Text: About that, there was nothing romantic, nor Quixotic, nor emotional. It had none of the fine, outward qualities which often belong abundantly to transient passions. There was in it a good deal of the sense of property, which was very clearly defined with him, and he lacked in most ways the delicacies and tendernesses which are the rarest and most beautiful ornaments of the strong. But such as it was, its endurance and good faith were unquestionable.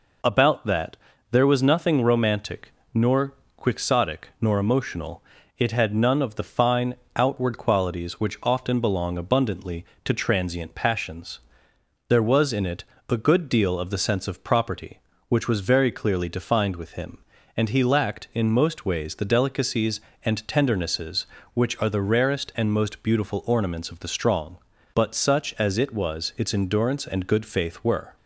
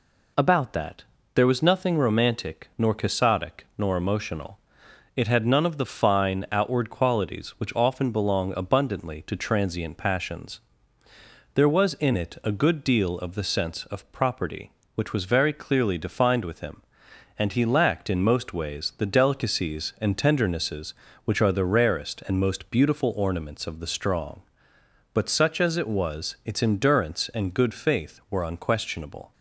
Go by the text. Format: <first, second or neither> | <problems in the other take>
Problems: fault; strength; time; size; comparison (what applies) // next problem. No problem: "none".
second | pauses between "nor" and "Quixotic"; slight; at 3.3 s; 0.22 s long // pauses between "it" and "a"; slight; at 12.8 s; 0.26 s long // stops before "unquestionable"; at 28.1 s